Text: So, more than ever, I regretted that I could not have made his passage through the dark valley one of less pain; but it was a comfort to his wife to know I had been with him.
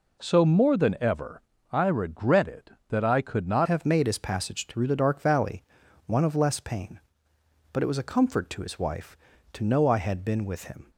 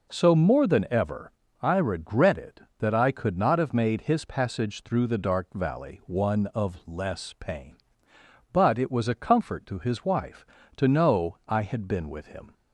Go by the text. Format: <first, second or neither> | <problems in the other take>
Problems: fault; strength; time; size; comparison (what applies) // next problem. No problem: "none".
second | changes voice at "have"; from 3.6 s on; 7.3 s long // pauses between "valley" and "one"; at 5.6 s; 0.44 s long